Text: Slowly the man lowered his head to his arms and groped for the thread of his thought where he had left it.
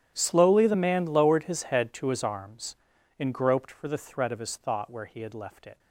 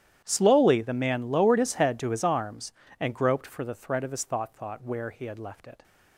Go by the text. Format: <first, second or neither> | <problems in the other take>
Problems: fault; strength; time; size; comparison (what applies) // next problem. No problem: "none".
first | starts louder than the rest; strong; until 1.2 s; 10.5 dB; strong in the first // says "thought" twice; at 4.5 s